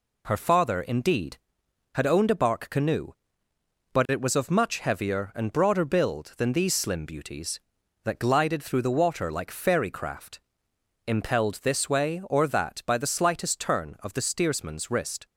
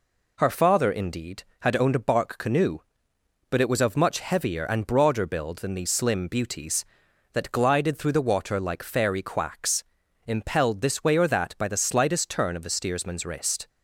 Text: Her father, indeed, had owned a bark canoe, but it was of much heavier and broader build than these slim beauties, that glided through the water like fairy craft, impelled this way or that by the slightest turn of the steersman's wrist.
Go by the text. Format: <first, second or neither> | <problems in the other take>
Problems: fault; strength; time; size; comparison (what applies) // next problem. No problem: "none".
first | says "quacks" for "craft"; at 9.2 s